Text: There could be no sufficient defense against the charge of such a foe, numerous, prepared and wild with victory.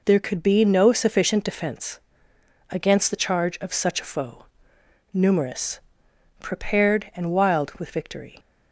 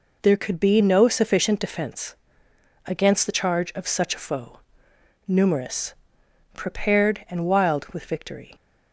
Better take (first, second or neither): neither